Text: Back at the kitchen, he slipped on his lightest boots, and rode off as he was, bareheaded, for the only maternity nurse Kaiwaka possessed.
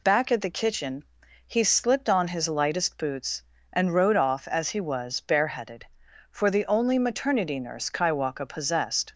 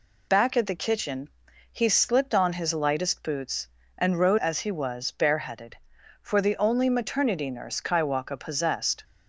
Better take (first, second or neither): first